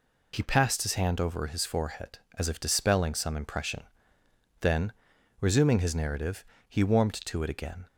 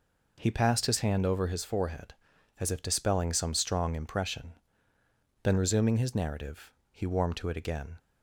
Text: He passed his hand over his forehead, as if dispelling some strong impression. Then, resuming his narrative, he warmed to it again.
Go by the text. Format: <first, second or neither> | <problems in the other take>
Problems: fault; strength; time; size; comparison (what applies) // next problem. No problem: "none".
second | skips "strong"; at 3.3 s